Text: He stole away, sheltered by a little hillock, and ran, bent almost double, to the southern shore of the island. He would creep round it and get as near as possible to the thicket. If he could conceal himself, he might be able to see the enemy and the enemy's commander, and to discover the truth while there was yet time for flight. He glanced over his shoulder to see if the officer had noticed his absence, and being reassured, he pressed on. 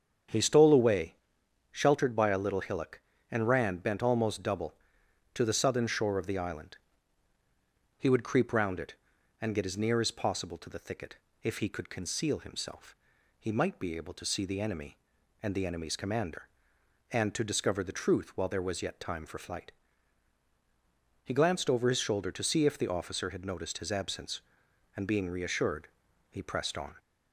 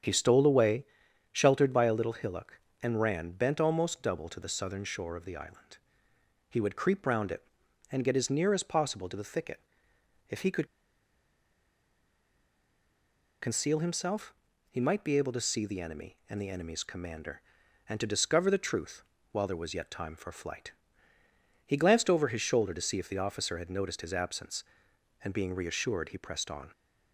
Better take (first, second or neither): first